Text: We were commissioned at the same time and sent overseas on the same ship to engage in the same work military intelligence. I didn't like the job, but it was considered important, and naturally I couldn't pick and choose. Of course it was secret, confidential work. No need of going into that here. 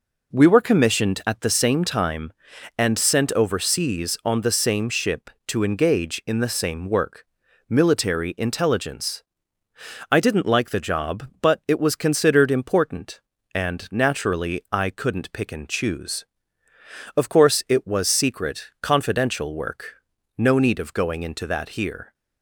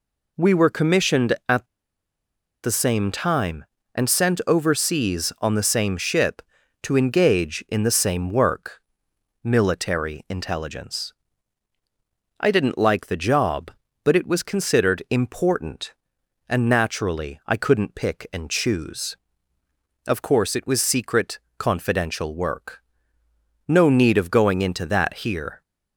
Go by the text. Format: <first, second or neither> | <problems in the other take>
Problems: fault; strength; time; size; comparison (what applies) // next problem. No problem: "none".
first | pauses between "at" and "the"; noticeable; at 1.6 s; 0.97 s long // pauses between "work" and "military"; noticeable; at 8.7 s; 0.62 s long; also in the first